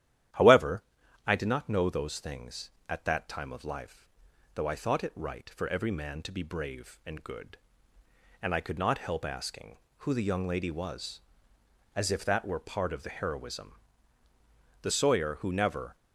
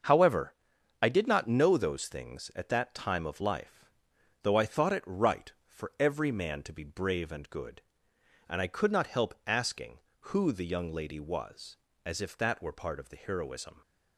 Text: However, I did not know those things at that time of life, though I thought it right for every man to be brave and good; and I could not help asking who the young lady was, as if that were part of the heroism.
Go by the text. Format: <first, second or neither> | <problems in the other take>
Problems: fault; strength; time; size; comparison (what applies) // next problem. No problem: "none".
second | starts louder than the rest; strong; until 1.7 s; 11.5 dB; also in the second // goes on to say "The Sawyer who never"; noticeable; from 14.7 s on; 1.1 s long